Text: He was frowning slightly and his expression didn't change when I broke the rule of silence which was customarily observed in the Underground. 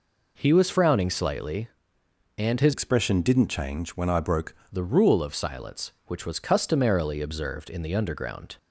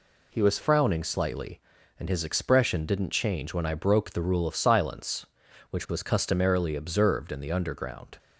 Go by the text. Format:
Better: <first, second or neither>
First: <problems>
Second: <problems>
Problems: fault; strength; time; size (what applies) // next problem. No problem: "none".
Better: second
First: changes voice from "expression" to "broke"; from 2.7 to 4.5 s; 1.8 s long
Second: none